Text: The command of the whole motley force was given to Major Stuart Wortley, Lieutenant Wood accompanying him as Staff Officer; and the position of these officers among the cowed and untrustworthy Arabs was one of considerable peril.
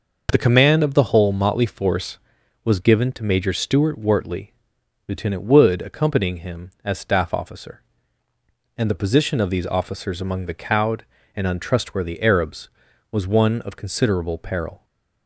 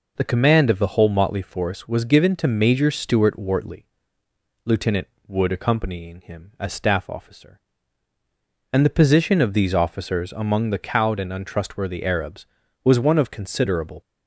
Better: first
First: none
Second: pauses between "Lieutenant" and "Wood"; slight; at 5.0 s; 0.18 s long // stops before "peril"; at 14.0 s

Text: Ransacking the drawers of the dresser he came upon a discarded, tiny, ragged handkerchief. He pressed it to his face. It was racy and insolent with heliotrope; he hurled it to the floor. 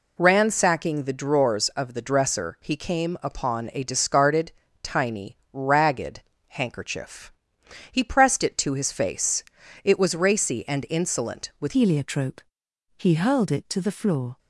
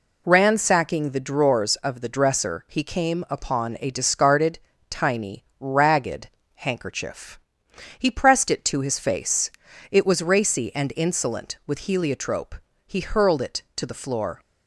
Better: second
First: pauses between "ragged" and "handkerchief"; slight; at 6.2 s; 0.26 s long // changes voice at "heliotrope"; from 11.7 s on; 2.6 s long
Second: pauses between "ragged" and "handkerchief"; slight; at 6.2 s; 0.26 s long

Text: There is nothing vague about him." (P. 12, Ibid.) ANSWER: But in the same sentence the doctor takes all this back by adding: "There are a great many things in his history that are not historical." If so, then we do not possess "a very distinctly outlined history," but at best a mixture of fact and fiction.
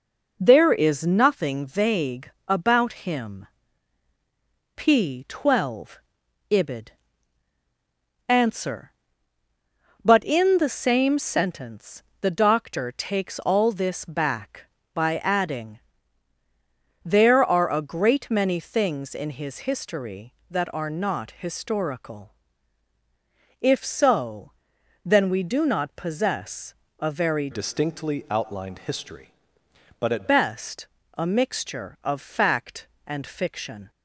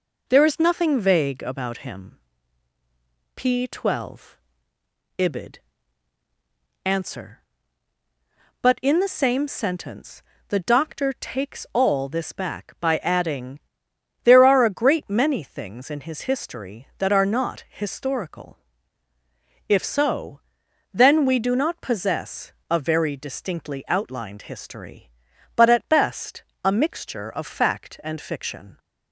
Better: second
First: pauses between "vague" and "about"; slight; at 2.2 s; 0.18 s long // pauses between "sentence" and "the"; slight; at 12.0 s; 0.18 s long // pauses between "possess" and "a"; slight; at 26.7 s; 0.24 s long // changes voice from "distinctly" to "at"; from 27.5 to 30.2 s; 2.7 s long // pauses between "best" and "a"; slight; at 30.8 s; 0.30 s long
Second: pauses between "sentence" and "the"; slight; at 10.2 s; 0.26 s long // pauses between "possess" and "a"; slight; at 22.5 s; 0.20 s long // pauses between "best" and "a"; slight; at 26.4 s; 0.20 s long

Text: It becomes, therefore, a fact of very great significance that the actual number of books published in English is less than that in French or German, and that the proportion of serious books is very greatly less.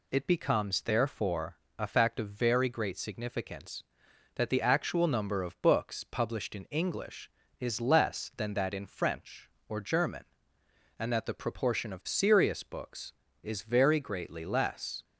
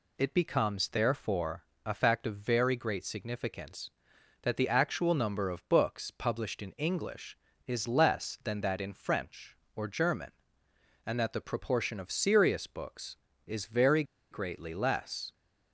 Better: first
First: none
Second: pauses between "very" and "greatly"; slight; at 14.0 s; 0.27 s long

